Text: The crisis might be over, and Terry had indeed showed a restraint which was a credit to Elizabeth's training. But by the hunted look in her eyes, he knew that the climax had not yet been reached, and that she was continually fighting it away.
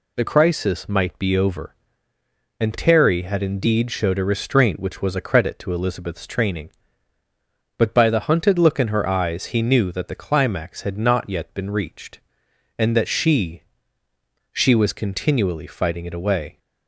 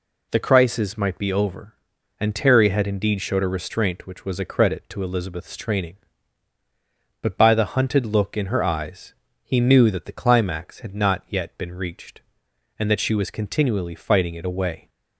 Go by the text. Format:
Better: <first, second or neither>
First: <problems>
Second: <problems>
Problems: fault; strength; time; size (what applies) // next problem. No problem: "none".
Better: second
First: says "she" twice; at 14.5 s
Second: none